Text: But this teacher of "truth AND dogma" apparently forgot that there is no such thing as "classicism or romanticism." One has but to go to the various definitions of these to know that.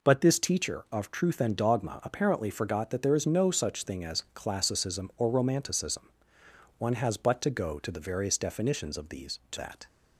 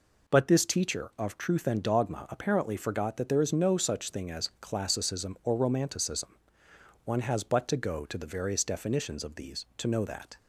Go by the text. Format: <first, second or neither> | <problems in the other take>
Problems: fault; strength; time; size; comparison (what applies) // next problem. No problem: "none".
second | skips "know"; at 9.5 s